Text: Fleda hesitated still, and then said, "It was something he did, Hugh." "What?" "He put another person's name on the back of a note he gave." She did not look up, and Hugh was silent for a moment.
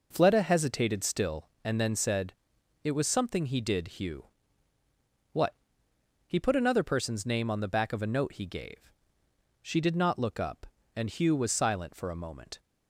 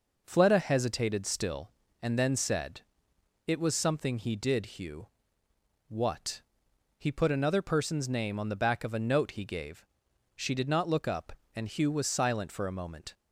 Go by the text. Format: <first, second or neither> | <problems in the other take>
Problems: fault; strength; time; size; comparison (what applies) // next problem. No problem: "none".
neither | none